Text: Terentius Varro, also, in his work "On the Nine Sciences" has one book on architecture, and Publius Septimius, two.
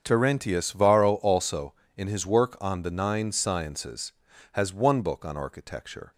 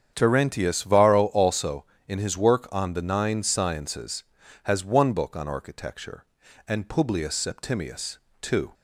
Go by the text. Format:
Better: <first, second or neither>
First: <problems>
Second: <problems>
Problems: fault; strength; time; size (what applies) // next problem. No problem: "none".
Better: second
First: starts louder than the rest; until 1.0 s; 7 dB // stops before "and Publius Septimius two"; at 6.1 s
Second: starts louder than the rest; strong; until 1.1 s; 8 dB